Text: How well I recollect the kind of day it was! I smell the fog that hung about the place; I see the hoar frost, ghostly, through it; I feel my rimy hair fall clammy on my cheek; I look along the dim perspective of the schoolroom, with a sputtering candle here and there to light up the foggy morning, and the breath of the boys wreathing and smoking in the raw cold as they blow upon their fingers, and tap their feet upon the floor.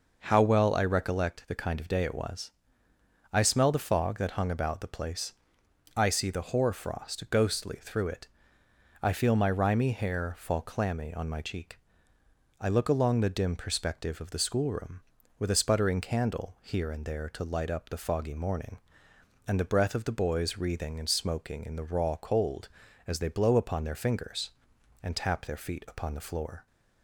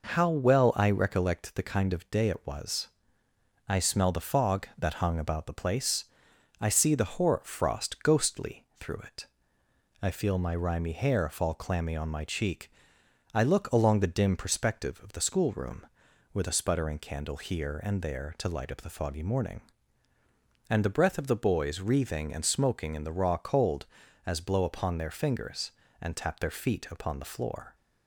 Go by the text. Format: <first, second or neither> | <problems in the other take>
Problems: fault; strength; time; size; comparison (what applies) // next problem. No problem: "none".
first | skips "they"; at 24.3 s